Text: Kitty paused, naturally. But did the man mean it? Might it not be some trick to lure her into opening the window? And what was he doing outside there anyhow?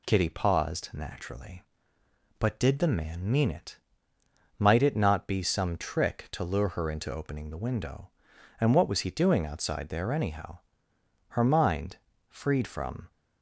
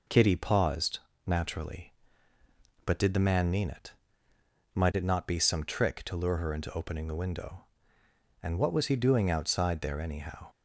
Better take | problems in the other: second | goes on to say "Her mind freed from"; strong; from 11.2 s on; 1.8 s long

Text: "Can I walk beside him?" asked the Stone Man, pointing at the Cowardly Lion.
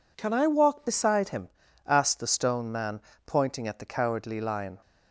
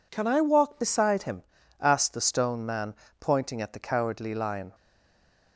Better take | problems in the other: first | stays silent after the last word; slight; from 4.7 s on; 0.8 s long

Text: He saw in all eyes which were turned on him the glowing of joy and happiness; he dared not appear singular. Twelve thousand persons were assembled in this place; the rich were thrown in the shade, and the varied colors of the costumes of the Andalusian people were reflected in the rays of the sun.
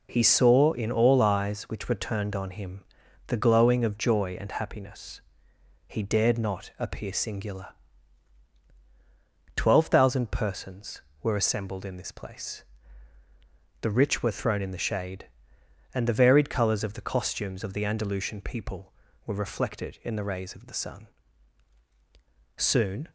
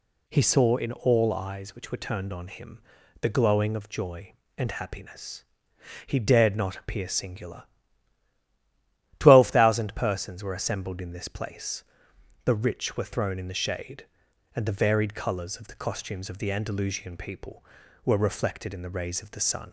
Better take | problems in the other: second | pauses between "him" and "the"; noticeable; at 2.8 s; 0.46 s long; also in the second // goes on to say "Soon"; from 22.5 s on; 0.54 s long

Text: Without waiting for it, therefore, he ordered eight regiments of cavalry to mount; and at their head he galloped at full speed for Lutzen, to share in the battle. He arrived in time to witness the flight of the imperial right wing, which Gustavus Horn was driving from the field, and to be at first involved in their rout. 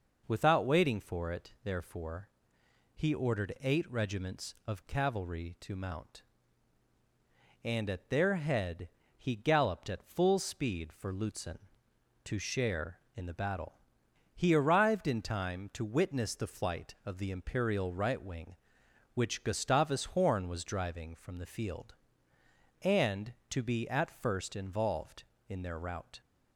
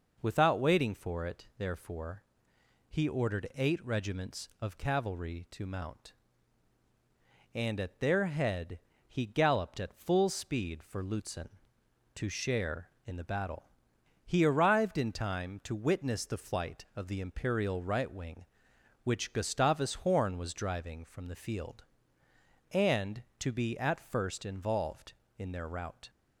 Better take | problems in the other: neither | pauses between "head" and "he"; slight; the same in both

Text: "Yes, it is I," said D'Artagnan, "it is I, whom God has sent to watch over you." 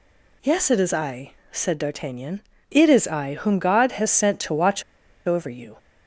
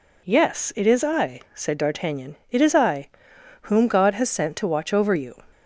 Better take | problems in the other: second | pauses between "watch" and "over"; at 4.8 s; 0.44 s long

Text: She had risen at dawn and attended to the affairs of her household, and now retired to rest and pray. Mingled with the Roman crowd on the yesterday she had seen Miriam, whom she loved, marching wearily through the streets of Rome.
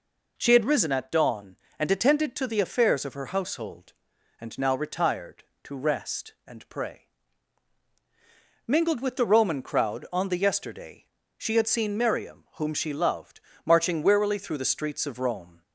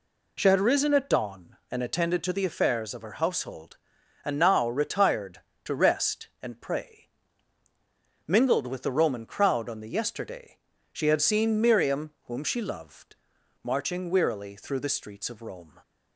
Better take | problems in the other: neither | pauses between "yesterday" and "she"; slight; the same in both

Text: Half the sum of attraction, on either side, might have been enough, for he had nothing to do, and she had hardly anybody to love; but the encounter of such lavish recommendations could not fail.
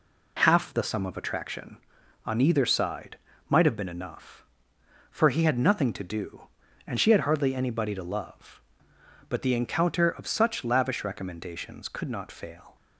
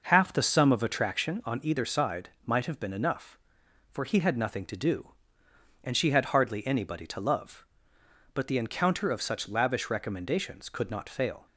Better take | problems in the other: first | starts louder than the rest; noticeable; until 1.4 s; 5.5 dB

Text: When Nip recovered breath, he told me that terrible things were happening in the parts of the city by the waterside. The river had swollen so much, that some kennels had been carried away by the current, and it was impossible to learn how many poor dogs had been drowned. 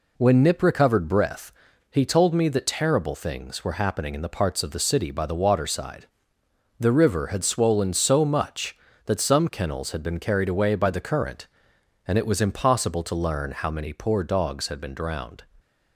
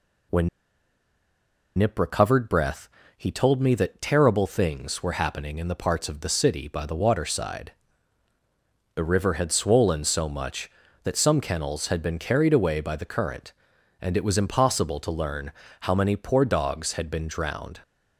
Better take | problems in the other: first | pauses between "When" and "Nip"; strong; at 0.4 s; 1.3 s long // pauses between "learn" and "how"; slight; at 15.5 s; 0.28 s long

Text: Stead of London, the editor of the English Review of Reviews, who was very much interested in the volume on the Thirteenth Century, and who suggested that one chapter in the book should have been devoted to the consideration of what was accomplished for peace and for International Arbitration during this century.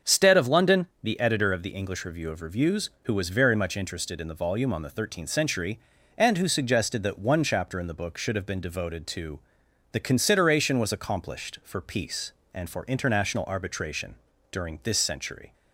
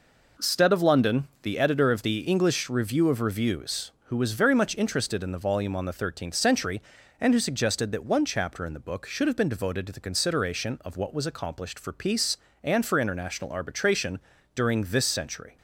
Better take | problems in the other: second | starts louder than the rest; until 1.1 s; 6.5 dB // pauses between "to" and "the"; noticeable; at 9.3 s; 0.54 s long // skips "of what"; at 10.7 s // pauses between "Arbitration" and "during"; slight; at 14.1 s; 0.36 s long; slight in the second

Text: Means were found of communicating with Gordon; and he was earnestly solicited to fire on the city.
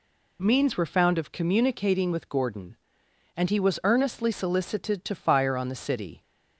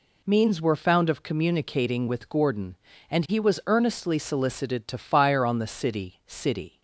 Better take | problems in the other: first | says "city" twice; at 6.2 s

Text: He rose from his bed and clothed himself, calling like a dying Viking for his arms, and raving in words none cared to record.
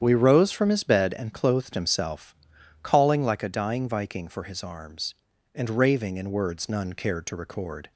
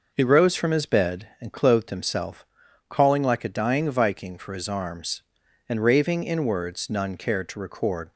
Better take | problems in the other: second | starts louder than the rest; strong; until 1.0 s; 9 dB // says "We" for "He"; at 0.0 s

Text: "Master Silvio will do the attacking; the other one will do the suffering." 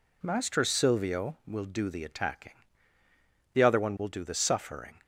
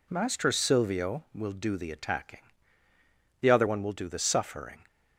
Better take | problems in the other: neither | none

